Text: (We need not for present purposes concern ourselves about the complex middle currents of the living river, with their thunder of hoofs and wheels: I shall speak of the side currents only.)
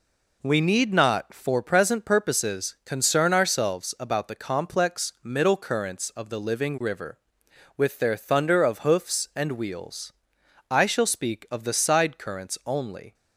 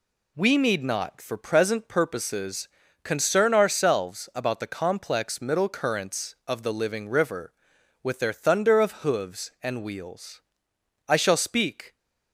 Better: first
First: none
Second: pauses between "purposes" and "concern"; slight; at 2.6 s; 0.34 s long // stops before "of the side currents only"; at 11.9 s

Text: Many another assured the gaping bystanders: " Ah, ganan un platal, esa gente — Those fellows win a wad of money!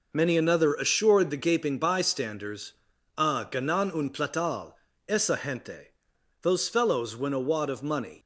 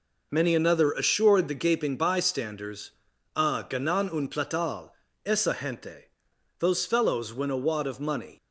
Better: neither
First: none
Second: none

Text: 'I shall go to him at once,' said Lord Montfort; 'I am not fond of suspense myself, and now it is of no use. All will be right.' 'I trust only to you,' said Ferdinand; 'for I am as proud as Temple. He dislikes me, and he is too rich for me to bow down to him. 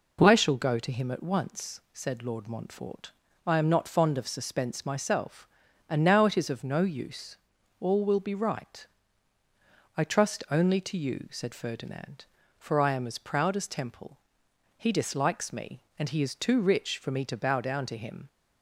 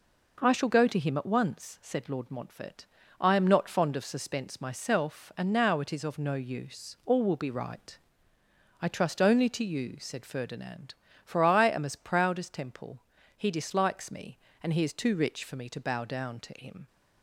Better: neither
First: none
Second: none

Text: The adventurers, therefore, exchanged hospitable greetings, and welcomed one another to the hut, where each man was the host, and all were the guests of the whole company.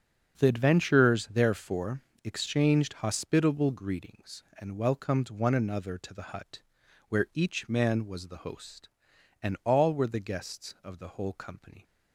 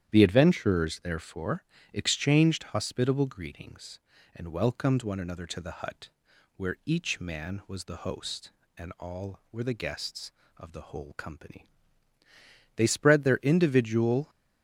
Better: first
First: starts louder than the rest; until 1.3 s; 6.5 dB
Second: starts louder than the rest; strong; until 1.1 s; 10 dB // goes on to say "They spread their individual"; from 12.7 s on; 1.5 s long

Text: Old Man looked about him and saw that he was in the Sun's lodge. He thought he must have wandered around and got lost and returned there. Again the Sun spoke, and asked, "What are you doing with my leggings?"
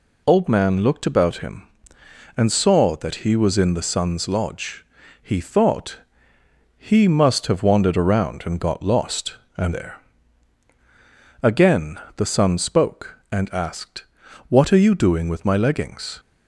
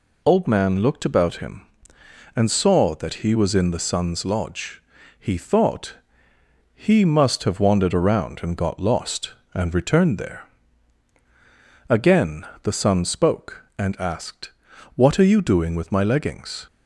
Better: second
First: pauses between "thought" and "he"; noticeable; at 5.9 s; 0.80 s long // skips "returned"; at 9.7 s // pauses between "Again" and "the"; slight; at 11.9 s; 0.18 s long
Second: pauses between "thought" and "he"; noticeable; at 5.9 s; 0.80 s long // pauses between "Again" and "the"; slight; at 12.4 s; 0.18 s long

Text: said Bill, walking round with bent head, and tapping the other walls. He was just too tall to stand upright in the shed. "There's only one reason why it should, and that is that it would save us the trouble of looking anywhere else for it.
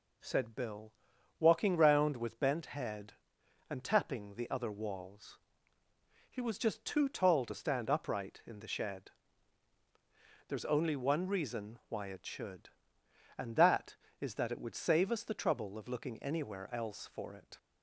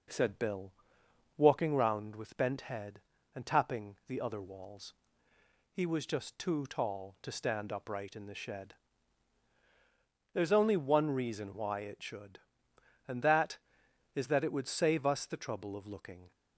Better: first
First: none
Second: stops before "anywhere else for it"; at 16.3 s

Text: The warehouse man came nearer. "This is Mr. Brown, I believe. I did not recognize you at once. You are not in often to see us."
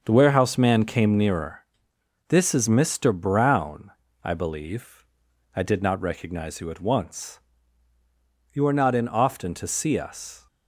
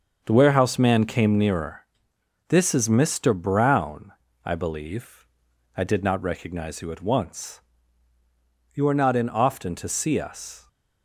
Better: neither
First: starts louder than the rest; until 1.0 s; 6.5 dB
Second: starts louder than the rest; until 1.2 s; 6.5 dB

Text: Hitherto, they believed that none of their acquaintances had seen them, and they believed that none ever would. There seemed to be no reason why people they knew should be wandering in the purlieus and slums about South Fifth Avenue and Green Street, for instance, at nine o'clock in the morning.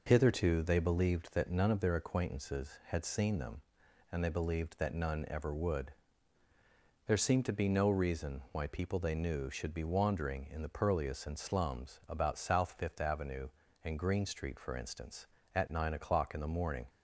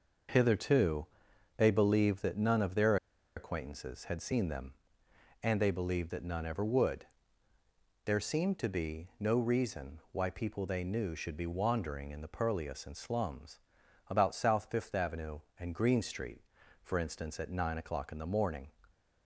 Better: first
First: none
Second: pauses between "their" and "acquaintances"; at 2.9 s; 0.40 s long // pauses between "slums" and "about"; noticeable; at 13.5 s; 0.48 s long

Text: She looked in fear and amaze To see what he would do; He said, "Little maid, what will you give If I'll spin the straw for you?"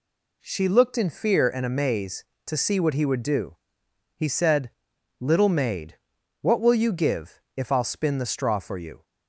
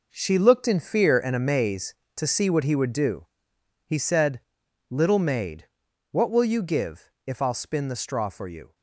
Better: first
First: none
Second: gets quieter; strong; throughout; 10.5 dB

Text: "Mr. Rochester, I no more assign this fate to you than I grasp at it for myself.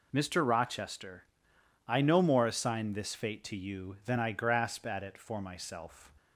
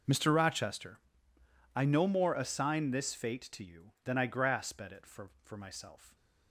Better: first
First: none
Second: says "for" twice; at 5.4 s

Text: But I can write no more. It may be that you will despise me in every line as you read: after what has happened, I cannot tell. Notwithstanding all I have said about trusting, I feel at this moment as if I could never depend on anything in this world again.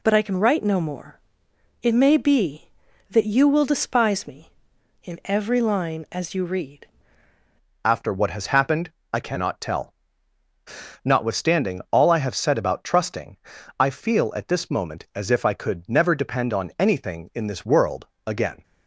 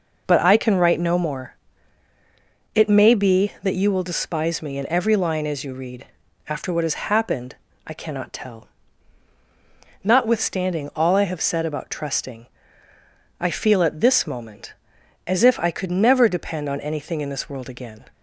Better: second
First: changes voice at "after"; from 7.8 s on; 10.8 s long // pauses between "world" and "again"; slight; at 18.0 s; 0.20 s long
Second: none

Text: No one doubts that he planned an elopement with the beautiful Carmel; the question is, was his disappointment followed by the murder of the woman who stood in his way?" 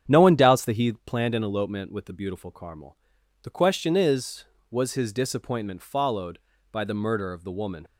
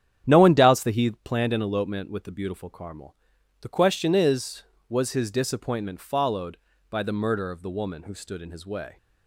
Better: second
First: starts louder than the rest; strong; until 1.0 s; 8.5 dB // stops before "who stood in his way"; at 7.8 s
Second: starts louder than the rest; strong; until 1.2 s; 9 dB

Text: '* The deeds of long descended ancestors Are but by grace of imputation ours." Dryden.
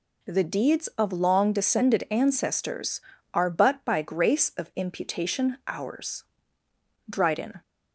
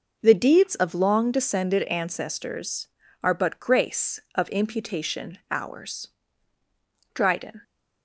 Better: first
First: none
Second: skips "by"; at 3.6 s

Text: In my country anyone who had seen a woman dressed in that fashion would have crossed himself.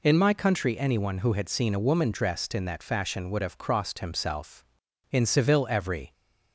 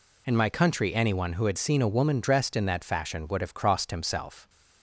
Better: second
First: goes on to say "In Seville every"; noticeable; from 5.1 s on; 1.0 s long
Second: none

